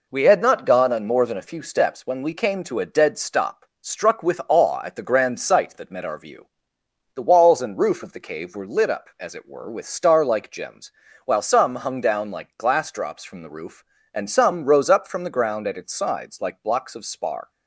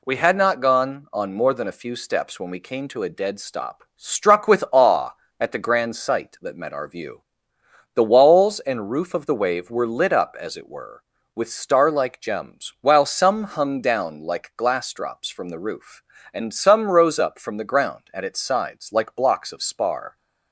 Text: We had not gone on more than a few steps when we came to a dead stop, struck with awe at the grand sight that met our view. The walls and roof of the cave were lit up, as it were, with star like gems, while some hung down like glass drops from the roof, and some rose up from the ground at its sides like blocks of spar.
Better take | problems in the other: first | says "wave" for "cave"; at 9.3 s

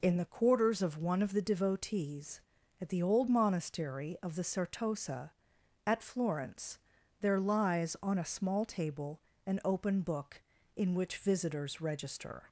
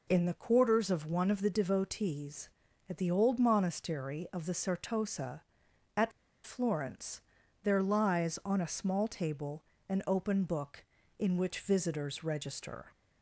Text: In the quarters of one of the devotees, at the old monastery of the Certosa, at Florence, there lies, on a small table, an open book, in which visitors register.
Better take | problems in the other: first | pauses between "at" and "Florence"; slight; at 6.1 s; 0.35 s long

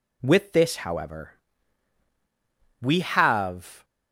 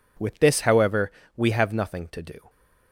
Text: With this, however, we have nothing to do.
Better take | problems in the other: second | stops before "nothing to do"; at 3.8 s

